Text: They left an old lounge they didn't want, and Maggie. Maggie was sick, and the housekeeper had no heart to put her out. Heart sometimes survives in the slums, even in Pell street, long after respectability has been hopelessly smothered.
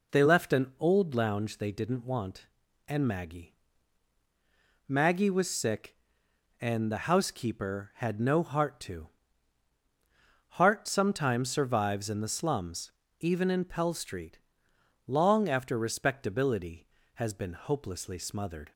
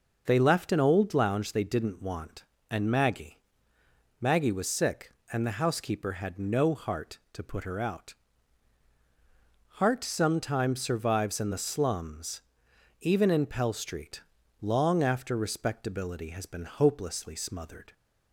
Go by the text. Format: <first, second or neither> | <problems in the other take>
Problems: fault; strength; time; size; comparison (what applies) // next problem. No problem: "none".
second | skips "put her out"; at 9.8 s